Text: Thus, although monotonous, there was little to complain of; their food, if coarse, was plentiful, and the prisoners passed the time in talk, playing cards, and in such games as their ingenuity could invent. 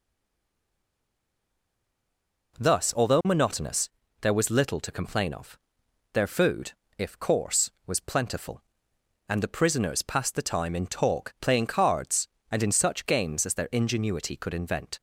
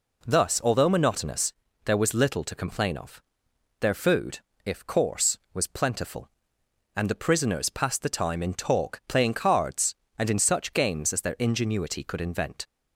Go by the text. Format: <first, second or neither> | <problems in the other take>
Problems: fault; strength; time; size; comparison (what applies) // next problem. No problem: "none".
second | stays silent before the first word; strong; until 2.5 s; 2.5 s long